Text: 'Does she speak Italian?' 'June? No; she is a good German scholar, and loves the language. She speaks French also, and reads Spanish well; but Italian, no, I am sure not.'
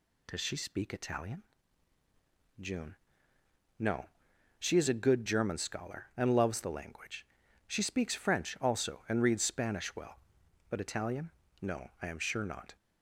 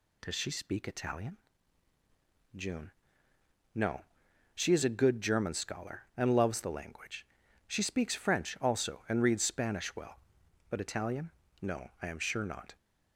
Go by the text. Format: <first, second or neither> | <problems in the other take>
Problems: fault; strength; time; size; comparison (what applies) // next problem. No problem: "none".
neither | none